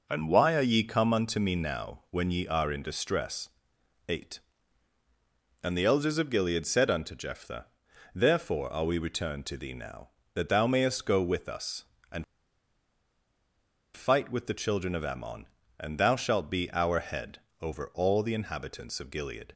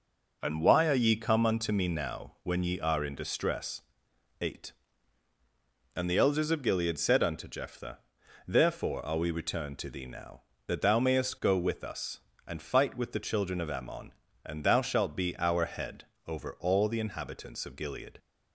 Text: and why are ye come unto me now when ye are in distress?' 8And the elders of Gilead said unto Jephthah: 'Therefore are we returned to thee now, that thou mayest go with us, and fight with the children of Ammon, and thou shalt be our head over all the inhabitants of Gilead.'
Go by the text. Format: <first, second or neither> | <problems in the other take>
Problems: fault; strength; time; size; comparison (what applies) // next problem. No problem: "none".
second | pauses between "and" and "fight"; strong; at 12.2 s; 1.7 s long // pauses between "head" and "over"; slight; at 17.4 s; 0.20 s long; slight in the second